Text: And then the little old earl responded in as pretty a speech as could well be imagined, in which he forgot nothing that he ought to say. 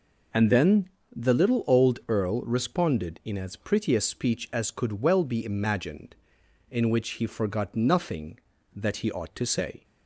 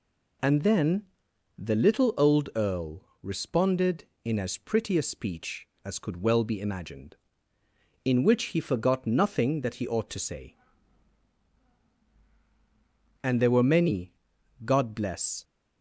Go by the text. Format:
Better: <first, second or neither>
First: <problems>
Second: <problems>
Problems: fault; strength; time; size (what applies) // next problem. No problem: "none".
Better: first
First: pauses between "then" and "the"; slight; at 0.8 s; 0.26 s long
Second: pauses between "then" and "the"; noticeable; at 1.0 s; 0.54 s long // pauses between "earl" and "responded"; slight; at 3.0 s; 0.18 s long // goes on to say "And there were many God bless"; strong; from 13.2 s on; 2.2 s long